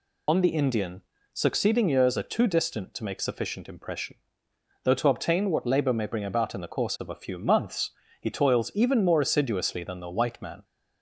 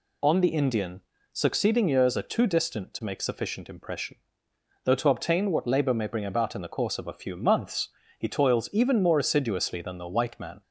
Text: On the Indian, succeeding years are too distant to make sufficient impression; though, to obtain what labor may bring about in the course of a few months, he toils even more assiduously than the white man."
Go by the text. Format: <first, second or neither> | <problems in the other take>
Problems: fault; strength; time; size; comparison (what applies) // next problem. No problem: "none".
second | loses the start of "On"; at 0.2 s; 55 ms